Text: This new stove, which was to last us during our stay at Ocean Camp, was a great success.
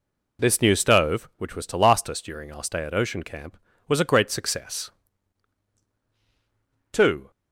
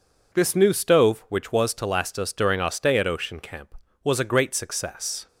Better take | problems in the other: second | goes on to say "Two"; slight; from 6.9 s on; 0.38 s long

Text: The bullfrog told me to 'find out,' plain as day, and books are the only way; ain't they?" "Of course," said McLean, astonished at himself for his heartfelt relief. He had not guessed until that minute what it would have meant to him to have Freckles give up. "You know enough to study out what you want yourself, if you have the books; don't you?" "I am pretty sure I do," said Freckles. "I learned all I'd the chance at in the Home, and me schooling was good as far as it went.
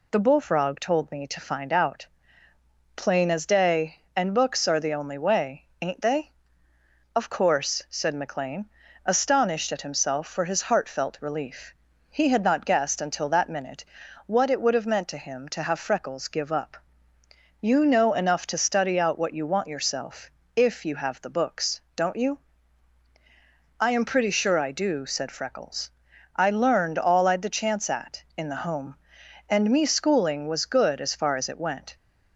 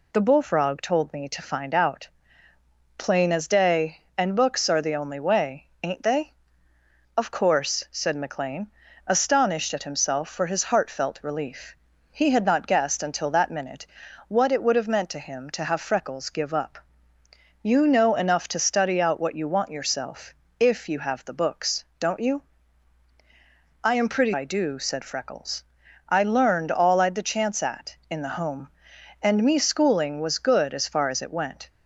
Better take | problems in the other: first | pauses between "minute" and "what"; at 13.8 s; 0.40 s long; also in the first // skips "sure"; at 24.3 s

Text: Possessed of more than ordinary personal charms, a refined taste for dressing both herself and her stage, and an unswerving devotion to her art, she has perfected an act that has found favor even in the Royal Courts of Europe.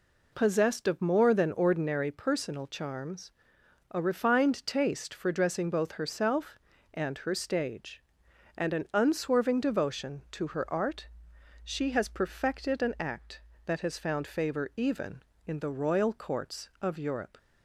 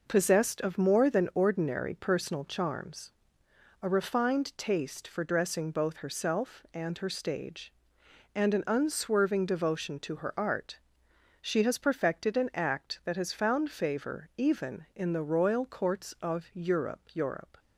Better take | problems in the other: first | says "Europe" twice; at 17.1 s

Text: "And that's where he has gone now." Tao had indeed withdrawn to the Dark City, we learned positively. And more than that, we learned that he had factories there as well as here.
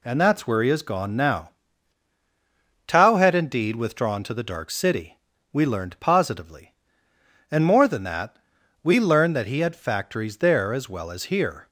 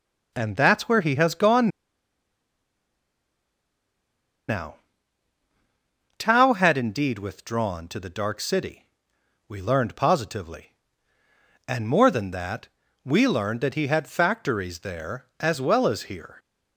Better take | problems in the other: first | pauses between "gone" and "now"; strong; at 1.6 s; 2.7 s long

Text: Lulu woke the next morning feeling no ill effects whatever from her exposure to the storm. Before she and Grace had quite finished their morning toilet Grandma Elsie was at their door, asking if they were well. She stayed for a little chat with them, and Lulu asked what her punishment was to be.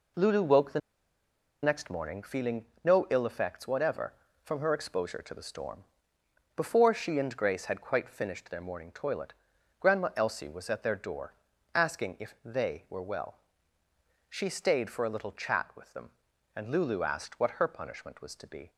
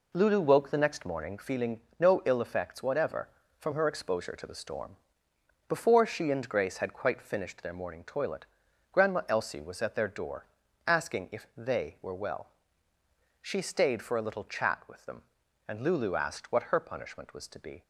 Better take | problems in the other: second | pauses between "the" and "next"; noticeable; at 0.7 s; 0.83 s long // pauses between "feeling" and "no"; slight; at 2.6 s; 0.18 s long; slight in the second // pauses between "toilet" and "Grandma"; noticeable; at 9.3 s; 0.46 s long; noticeable in the second

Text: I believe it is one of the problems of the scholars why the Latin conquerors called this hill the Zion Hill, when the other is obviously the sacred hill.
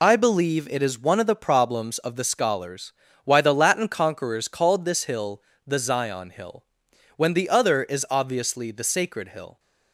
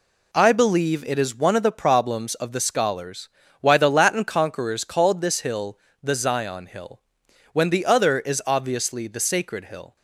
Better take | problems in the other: second | loses the start of "I"; at 0.0 s; 40 ms // pauses between "scholars" and "why"; slight; at 2.9 s; 0.32 s long; slight in the second // pauses between "hill" and "the"; slight; at 5.4 s; 0.24 s long; slight in the second

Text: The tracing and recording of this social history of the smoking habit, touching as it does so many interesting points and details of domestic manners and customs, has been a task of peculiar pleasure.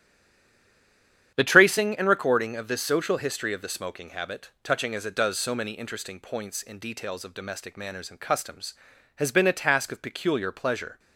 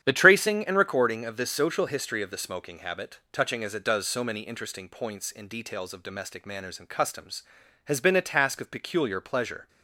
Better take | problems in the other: second | stays silent before the first word; noticeable; until 1.3 s; 1.3 s long // starts louder than the rest; strong; until 2.3 s; 9.5 dB; strong in the second

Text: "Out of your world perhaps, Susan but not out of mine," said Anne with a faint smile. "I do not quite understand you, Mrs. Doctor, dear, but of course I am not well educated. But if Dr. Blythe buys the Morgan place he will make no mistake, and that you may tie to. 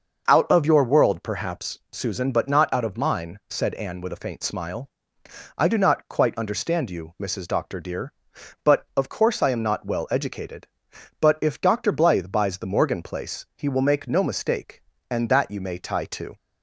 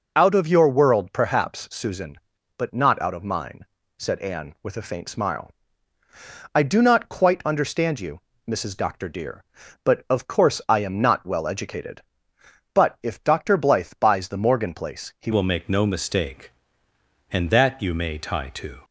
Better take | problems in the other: first | changes voice at "will"; from 15.3 s on; 3.5 s long

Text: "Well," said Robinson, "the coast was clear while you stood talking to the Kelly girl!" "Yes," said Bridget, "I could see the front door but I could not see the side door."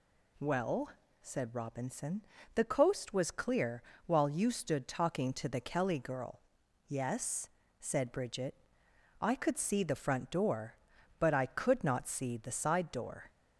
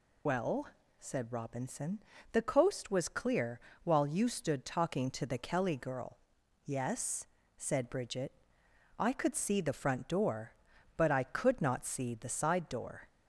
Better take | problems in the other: first | loses the start of "Well"; at 0.2 s; 125 ms // pauses between "clear" and "while"; slight; at 3.5 s; 0.24 s long; slight in the first

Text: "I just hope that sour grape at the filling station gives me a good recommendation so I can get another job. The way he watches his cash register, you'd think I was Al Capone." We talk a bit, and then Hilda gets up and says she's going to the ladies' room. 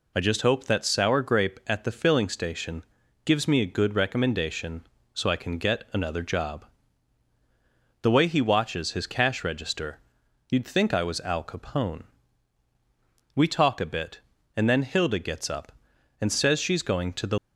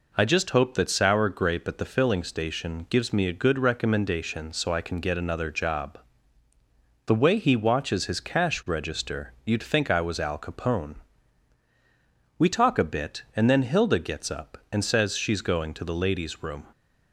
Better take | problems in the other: second | pauses between "station" and "gives"; at 2.8 s; 0.44 s long // stops before "ladies room"; at 17.3 s

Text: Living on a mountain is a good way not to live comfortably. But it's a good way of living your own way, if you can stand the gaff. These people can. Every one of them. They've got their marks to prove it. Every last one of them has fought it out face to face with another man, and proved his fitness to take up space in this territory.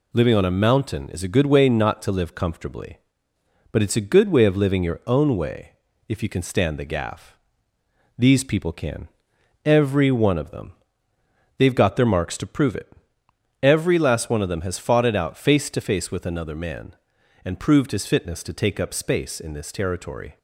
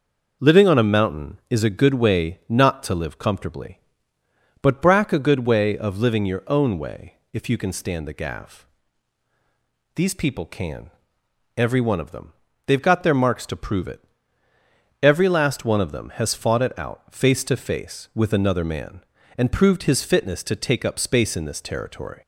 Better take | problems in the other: first | says "brack" for "it's"; at 4.8 s

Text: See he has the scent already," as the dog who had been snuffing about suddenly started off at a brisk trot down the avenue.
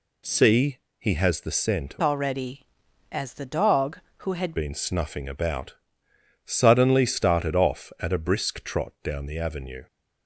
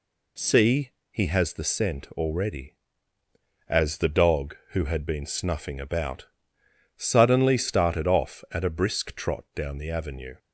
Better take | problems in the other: second | pauses between "See" and "he"; slight; at 0.7 s; 0.20 s long; slight in the second // changes voice from "already" to "had"; from 2.0 to 4.5 s; 2.5 s long // pauses between "about" and "suddenly"; noticeable; at 5.7 s; 0.70 s long; noticeable in the second

